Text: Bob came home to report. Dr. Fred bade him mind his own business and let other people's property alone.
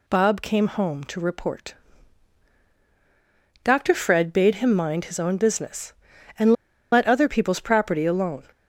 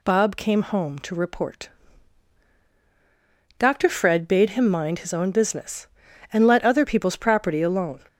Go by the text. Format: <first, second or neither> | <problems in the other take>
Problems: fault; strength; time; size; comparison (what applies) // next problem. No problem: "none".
second | pauses between "and" and "let"; at 6.5 s; 0.39 s long